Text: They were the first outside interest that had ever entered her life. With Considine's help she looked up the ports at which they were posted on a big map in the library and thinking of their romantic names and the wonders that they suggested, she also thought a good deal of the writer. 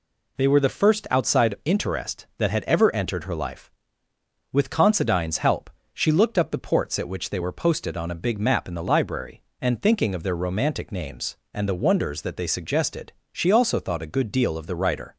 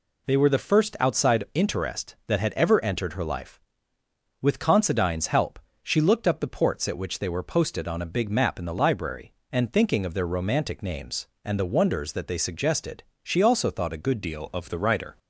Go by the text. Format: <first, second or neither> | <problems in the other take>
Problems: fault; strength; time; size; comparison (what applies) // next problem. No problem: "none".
first | pauses between "help" and "she"; slight; at 5.5 s; 0.24 s long; slight in the first // changes voice at "deal"; from 14.2 s on; 0.9 s long